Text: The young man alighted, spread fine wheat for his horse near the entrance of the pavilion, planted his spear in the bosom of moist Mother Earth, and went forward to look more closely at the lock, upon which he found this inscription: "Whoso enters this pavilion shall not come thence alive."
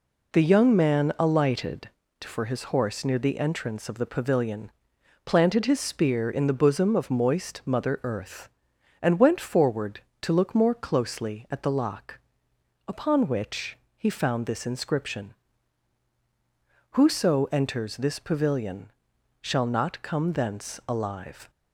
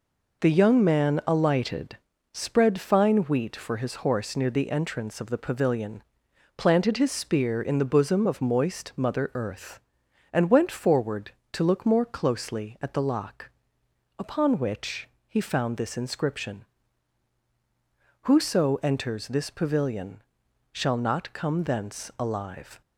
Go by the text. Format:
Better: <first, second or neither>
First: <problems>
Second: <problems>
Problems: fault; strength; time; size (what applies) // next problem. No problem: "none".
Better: second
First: skips "spread fine wheat"; at 2.0 s // pauses between "which" and "he"; slight; at 13.7 s; 0.22 s long // pauses between "pavilion" and "shall"; noticeable; at 18.8 s; 0.52 s long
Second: pauses between "which" and "he"; slight; at 15.0 s; 0.22 s long // pauses between "pavilion" and "shall"; noticeable; at 20.2 s; 0.52 s long